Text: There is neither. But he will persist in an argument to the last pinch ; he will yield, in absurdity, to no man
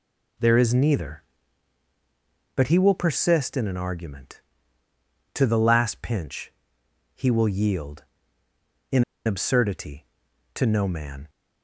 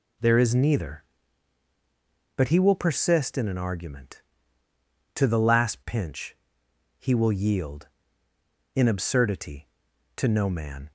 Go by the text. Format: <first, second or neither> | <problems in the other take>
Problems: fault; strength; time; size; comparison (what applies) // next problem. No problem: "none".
second | pauses between "in" and "absurdity"; slight; at 9.0 s; 0.22 s long